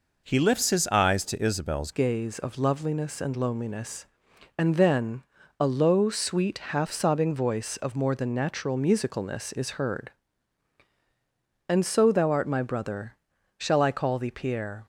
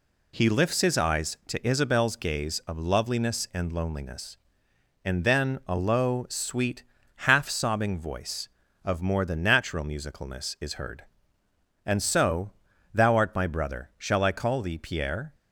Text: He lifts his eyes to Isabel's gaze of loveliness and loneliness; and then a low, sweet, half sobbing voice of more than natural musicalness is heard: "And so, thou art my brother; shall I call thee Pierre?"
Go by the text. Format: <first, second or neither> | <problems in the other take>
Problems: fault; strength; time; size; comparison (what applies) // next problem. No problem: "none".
second | changes voice at "gaze"; from 1.9 s on; 12.9 s long // pauses between "then" and "a"; at 5.2 s; 0.38 s long